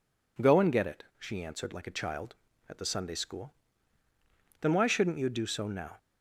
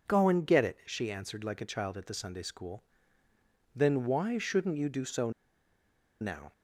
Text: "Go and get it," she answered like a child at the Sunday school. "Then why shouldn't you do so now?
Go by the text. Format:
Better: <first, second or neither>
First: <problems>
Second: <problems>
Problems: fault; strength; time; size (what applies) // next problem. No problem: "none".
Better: first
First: none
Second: pauses between "so" and "now"; noticeable; at 5.3 s; 0.89 s long